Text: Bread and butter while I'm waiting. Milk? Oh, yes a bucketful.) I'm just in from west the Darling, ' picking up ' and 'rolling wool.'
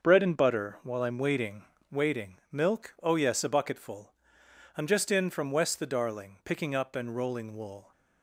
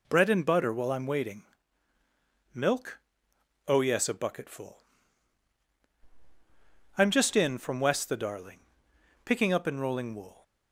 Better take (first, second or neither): second